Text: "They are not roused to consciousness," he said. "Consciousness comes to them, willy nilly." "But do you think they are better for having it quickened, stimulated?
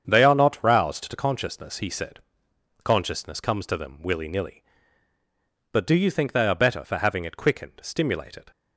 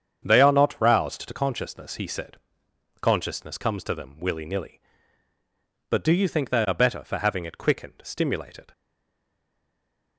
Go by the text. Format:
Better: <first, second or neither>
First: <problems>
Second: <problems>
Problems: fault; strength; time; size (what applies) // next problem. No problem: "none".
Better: first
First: starts louder than the rest; strong; until 1.0 s; 7.5 dB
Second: starts louder than the rest; strong; until 1.2 s; 8 dB // stays silent after the last word; noticeable; from 8.7 s on; 1.4 s long